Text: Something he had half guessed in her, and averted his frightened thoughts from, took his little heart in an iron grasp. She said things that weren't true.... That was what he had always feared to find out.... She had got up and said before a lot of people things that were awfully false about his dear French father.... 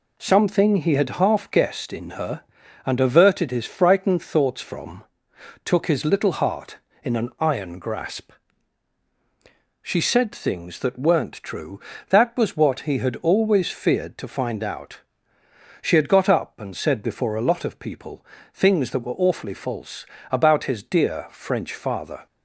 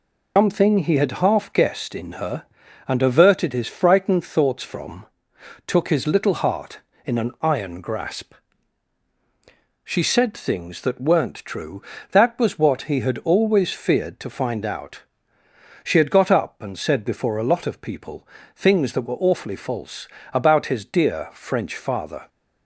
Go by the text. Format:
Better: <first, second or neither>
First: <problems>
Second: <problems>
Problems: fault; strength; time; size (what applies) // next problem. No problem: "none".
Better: first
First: pauses between "people" and "things"; slight; at 18.2 s; 0.26 s long // pauses between "false" and "about"; slight; at 20.0 s; 0.28 s long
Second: loses the start of "Something"; at 0.3 s; 160 ms // pauses between "people" and "things"; slight; at 18.2 s; 0.26 s long // pauses between "false" and "about"; slight; at 20.0 s; 0.28 s long